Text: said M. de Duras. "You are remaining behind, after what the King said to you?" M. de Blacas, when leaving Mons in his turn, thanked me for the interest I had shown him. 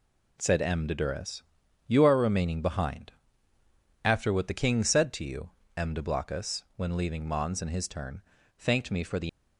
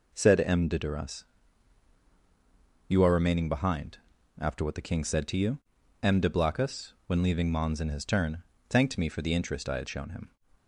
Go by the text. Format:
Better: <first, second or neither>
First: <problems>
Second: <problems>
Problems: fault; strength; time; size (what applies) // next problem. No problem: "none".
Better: second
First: stops before "interest I had shown him"; at 9.2 s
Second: none